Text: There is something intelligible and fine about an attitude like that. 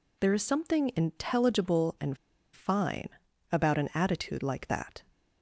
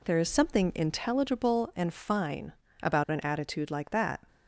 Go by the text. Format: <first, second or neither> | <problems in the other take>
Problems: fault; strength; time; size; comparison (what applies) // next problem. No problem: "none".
second | pauses between "and" and "fine"; at 2.1 s; 0.37 s long // pauses between "fine" and "about"; at 3.0 s; 0.42 s long; slight in the second